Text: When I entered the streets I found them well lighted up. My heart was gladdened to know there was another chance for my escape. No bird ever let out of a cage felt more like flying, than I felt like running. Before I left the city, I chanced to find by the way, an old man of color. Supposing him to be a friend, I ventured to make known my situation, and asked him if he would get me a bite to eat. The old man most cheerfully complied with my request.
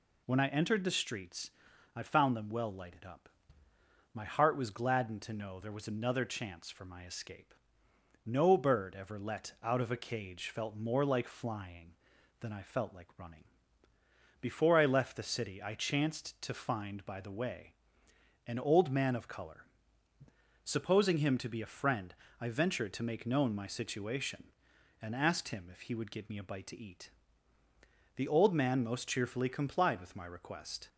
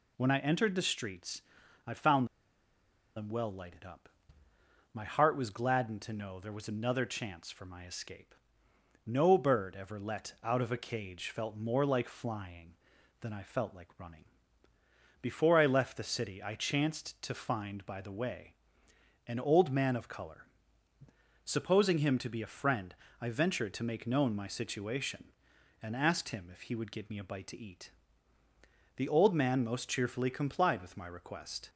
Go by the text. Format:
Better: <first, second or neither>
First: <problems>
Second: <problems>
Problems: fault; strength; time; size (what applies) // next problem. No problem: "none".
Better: first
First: pauses between "streets" and "I"; at 1.4 s; 0.44 s long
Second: pauses between "streets" and "I"; at 1.4 s; 0.44 s long // pauses between "found" and "them"; noticeable; at 2.2 s; 0.89 s long